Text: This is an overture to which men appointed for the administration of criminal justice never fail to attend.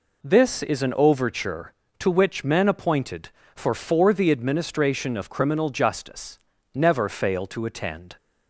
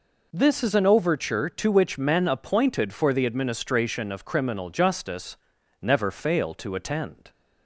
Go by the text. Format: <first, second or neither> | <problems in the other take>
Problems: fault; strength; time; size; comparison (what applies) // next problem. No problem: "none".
second | says "for" twice; at 3.7 s // pauses between "justice" and "never"; slight; at 6.3 s; 0.36 s long; also in the second